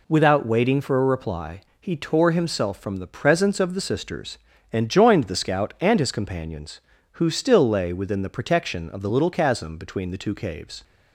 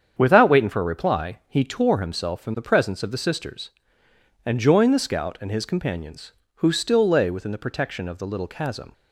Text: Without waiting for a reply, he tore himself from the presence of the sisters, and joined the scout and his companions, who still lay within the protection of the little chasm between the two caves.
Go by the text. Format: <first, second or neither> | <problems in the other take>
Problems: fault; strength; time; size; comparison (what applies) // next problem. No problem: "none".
first | starts louder than the rest; strong; until 1.1 s; 8 dB // stops before "between the two caves"; at 8.9 s